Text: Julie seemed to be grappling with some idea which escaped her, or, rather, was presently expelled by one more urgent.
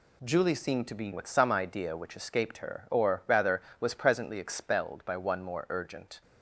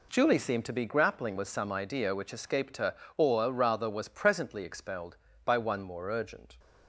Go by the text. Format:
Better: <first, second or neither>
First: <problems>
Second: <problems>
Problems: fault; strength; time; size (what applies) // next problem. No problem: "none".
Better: second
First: skips "grappling"; at 1.1 s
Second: none